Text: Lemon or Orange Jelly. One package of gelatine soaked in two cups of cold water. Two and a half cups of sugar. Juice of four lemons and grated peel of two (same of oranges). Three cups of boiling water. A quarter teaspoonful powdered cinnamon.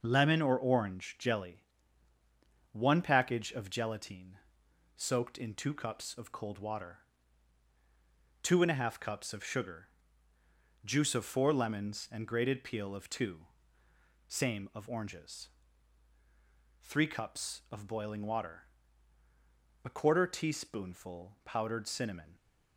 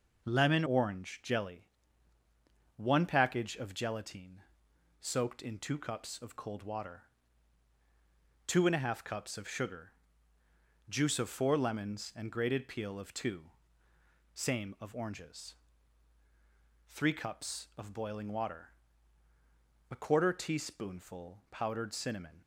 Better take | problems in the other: first | skips "or"; at 0.6 s // pauses between "gelatine" and "soaked"; noticeable; at 4.3 s; 0.60 s long; noticeable in the first

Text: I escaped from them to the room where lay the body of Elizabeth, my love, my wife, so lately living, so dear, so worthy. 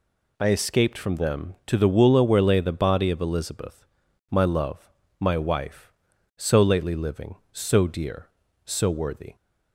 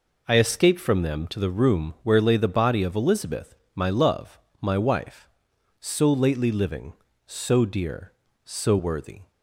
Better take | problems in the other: second | says "woola" for "room"; at 1.8 s

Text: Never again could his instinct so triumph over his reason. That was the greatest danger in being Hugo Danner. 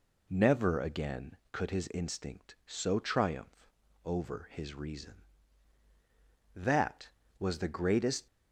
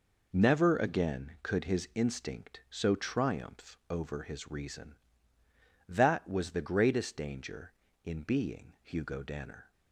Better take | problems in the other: second | pauses between "triumph" and "over"; slight; at 3.6 s; 0.34 s long // stops before "danger in being Hugo Danner"; at 8.2 s

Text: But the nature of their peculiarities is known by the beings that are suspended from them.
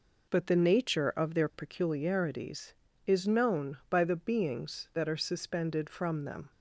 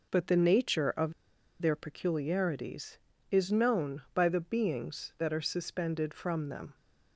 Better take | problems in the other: first | pauses between "of" and "their"; noticeable; at 1.1 s; 0.49 s long

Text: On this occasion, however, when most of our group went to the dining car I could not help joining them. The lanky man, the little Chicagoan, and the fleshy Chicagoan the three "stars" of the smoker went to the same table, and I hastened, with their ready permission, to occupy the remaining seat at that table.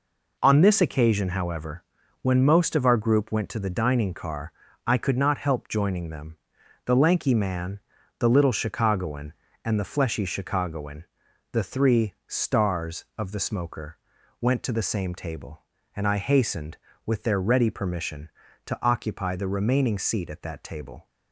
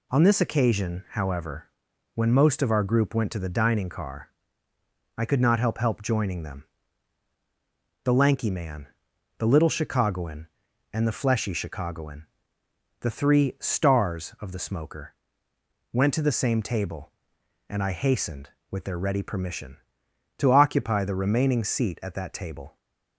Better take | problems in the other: first | pauses between "car" and "I"; noticeable; at 4.2 s; 0.88 s long; slight in the first // says "help" twice; at 5.7 s // pauses between "Chicagoan" and "the"; noticeable; at 12.2 s; 0.74 s long; noticeable in the first // pauses between "smoker" and "went"; noticeable; at 15.1 s; 0.76 s long; also in the first

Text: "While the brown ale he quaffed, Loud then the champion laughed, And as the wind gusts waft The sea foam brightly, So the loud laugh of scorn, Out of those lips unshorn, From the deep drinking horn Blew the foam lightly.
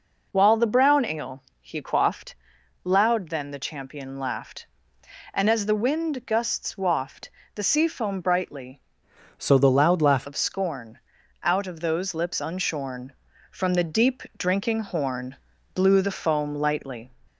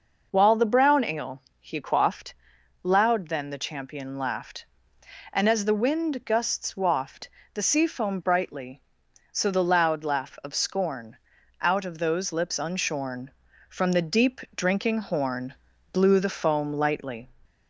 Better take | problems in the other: second | pauses between "ale" and "he"; slight; at 1.4 s; 0.16 s long; slight in the second // pauses between "waft" and "The"; slight; at 7.2 s; 0.26 s long; slight in the second // changes voice from "So" to "laugh"; from 9.3 to 10.2 s; 0.9 s long // pauses between "deep" and "drinking"; slight; at 14.2 s; 0.16 s long; slight in the second // pauses between "horn" and "Blew"; at 15.3 s; 0.38 s long; also in the second

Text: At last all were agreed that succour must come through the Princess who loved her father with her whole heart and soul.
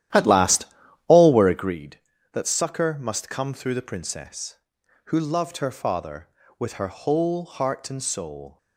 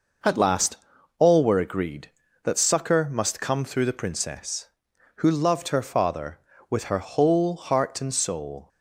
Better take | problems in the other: second | starts louder than the rest; strong; until 1.7 s; 12 dB // pauses between "last" and "all"; at 0.6 s; 0.42 s long; also in the second

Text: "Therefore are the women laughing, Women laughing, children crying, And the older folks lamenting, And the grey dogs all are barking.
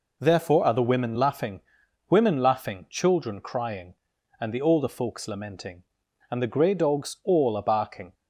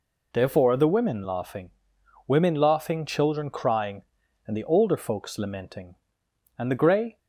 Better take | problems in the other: first | stops before "dogs all are barking"; at 7.1 s

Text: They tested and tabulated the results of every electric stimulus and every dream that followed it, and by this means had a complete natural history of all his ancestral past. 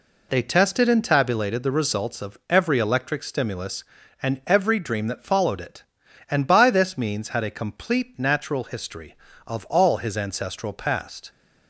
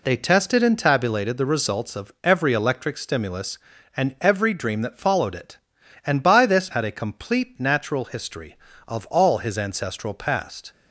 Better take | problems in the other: first | skips "means"; at 6.7 s

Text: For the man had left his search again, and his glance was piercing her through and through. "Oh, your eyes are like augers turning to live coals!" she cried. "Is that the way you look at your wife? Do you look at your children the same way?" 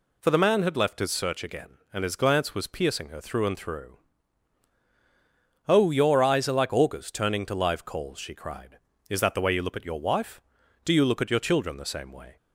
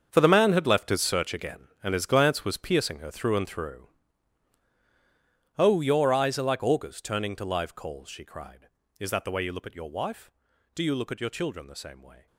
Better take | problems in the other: first | gets quieter; strong; throughout; 13.5 dB

